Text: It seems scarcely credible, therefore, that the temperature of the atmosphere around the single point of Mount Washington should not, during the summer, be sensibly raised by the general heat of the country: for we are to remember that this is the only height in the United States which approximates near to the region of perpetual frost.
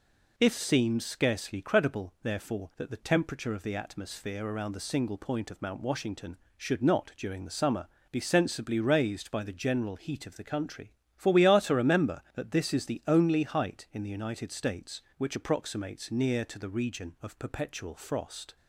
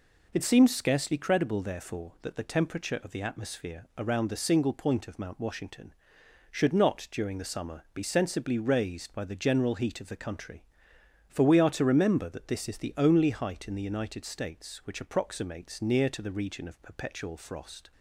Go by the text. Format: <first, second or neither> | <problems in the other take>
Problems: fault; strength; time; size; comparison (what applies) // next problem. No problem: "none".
second | says "If" for "It"; at 0.3 s